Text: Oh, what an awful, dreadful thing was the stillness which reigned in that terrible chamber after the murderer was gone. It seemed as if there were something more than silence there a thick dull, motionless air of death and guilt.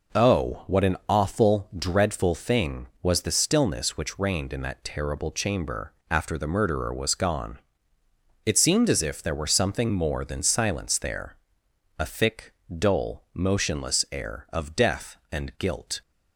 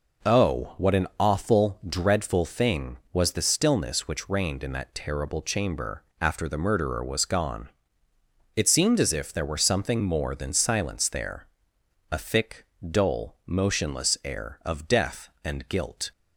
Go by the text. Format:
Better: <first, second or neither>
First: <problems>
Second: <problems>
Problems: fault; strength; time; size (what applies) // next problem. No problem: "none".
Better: neither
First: pauses between "chamber" and "after"; slight; at 5.9 s; 0.16 s long // pauses between "there" and "a"; noticeable; at 11.3 s; 0.60 s long // pauses between "thick" and "dull"; slight; at 12.5 s; 0.28 s long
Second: pauses between "chamber" and "after"; slight; at 6.0 s; 0.16 s long // pauses between "there" and "a"; noticeable; at 11.4 s; 0.62 s long // pauses between "thick" and "dull"; slight; at 12.6 s; 0.28 s long